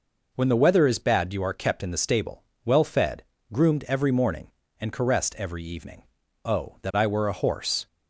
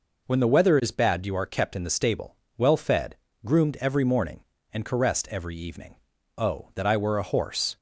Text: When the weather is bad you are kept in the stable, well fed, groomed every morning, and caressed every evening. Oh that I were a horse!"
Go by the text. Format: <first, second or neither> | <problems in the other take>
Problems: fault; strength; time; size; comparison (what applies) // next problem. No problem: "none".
neither | none